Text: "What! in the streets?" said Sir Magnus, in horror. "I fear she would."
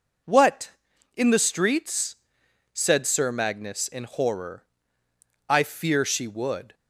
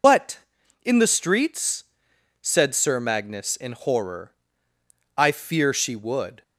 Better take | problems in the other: first | loses the start of "What"; at 0.0 s; 100 ms

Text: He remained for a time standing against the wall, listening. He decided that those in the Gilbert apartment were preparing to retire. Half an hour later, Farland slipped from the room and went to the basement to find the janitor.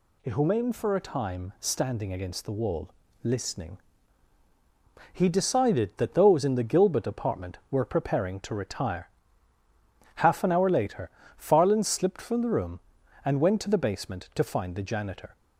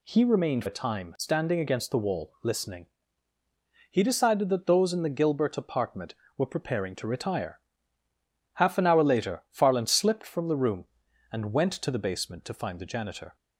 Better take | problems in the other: first | skips "for"; at 0.6 s

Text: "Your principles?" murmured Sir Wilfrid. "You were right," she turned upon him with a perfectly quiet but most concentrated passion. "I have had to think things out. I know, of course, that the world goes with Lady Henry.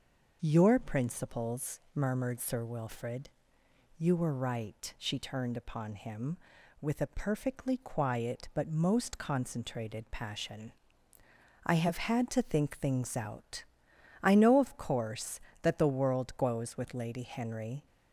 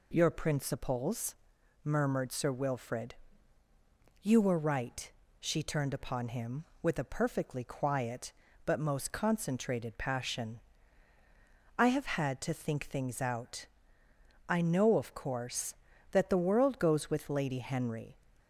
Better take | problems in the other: neither | none

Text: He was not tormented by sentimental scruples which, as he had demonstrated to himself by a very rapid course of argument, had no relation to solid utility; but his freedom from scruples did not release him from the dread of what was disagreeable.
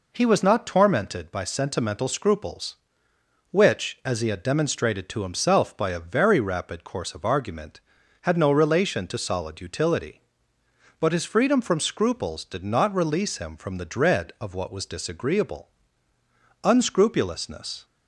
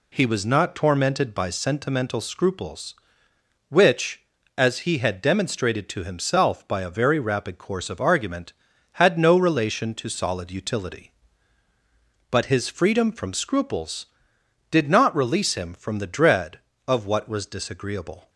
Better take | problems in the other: second | goes on to say "Unscrupulousness"; noticeable; from 16.6 s on; 1.2 s long

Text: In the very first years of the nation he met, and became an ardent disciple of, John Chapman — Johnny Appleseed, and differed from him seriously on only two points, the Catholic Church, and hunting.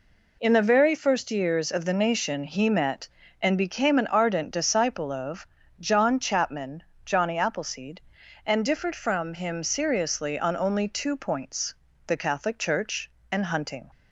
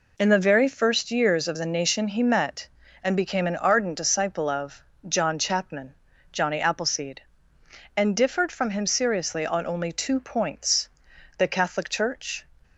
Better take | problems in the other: first | stops before "and hunting"; at 12.6 s

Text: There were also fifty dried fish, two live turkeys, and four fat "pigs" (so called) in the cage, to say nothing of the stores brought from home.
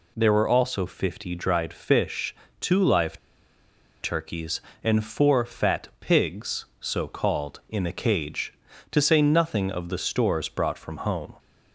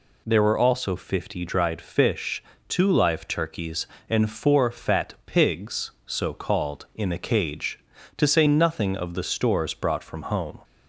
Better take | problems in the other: second | pauses between "live" and "turkeys"; noticeable; at 3.1 s; 0.83 s long

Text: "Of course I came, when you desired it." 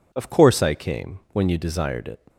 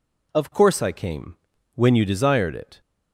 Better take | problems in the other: neither | none

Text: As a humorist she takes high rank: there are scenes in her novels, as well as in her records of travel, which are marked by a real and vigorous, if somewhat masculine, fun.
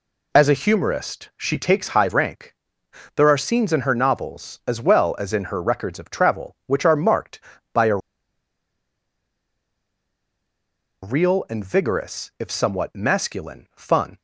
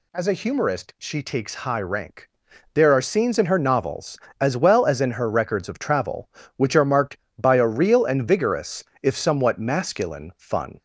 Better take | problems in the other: second | pauses between "a" and "real"; strong; at 7.9 s; 3.0 s long

